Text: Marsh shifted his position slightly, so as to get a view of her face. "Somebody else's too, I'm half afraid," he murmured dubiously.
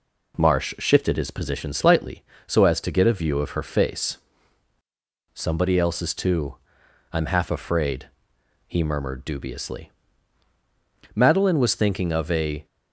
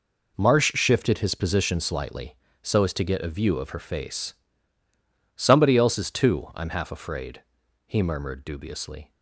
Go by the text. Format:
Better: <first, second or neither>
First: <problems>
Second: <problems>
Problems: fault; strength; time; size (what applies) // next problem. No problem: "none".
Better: second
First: goes on to say "Madeline was thinking of a"; from 11.1 s on; 1.5 s long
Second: none